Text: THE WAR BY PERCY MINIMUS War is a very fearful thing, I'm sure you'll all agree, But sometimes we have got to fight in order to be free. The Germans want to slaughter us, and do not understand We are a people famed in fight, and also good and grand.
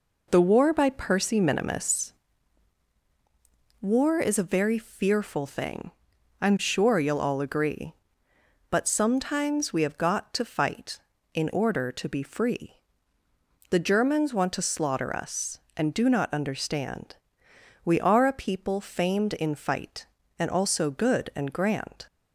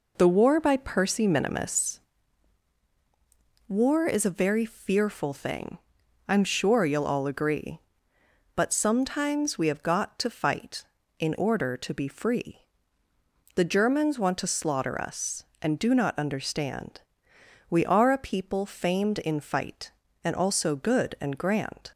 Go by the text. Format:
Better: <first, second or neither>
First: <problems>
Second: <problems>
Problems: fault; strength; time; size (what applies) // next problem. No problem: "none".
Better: neither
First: pauses between "MINIMUS" and "War"; strong; at 2.1 s; 1.6 s long // pauses between "understand" and "We"; noticeable; at 17.1 s; 0.68 s long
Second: pauses between "MINIMUS" and "War"; strong; at 2.0 s; 1.6 s long // pauses between "understand" and "We"; noticeable; at 17.0 s; 0.68 s long